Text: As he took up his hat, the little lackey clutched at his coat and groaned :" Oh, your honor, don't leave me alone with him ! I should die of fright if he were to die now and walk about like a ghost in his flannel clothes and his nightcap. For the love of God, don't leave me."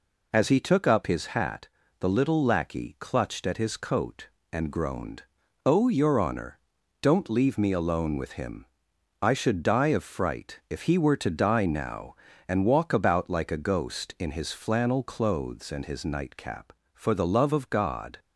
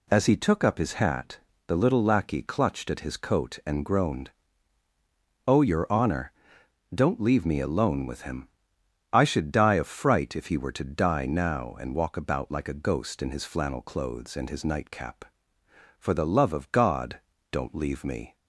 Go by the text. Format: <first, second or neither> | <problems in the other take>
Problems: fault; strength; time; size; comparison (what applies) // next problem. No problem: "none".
second | stops before "don't leave me"; at 18.1 s